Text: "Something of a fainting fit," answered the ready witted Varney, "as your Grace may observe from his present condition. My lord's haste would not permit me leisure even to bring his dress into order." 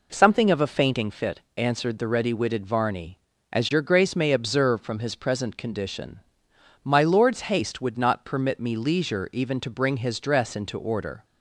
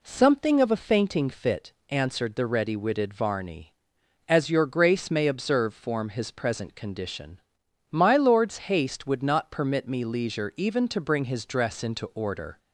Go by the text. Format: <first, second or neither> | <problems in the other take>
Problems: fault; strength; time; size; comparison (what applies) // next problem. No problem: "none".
first | says "form" for "from"; at 5.7 s // pauses between "lord's" and "haste"; slight; at 8.5 s; 0.16 s long